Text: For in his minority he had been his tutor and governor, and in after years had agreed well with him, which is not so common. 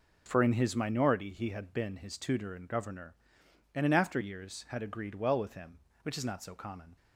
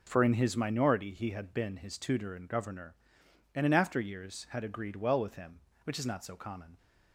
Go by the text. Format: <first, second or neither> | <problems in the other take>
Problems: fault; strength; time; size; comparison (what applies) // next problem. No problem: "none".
neither | none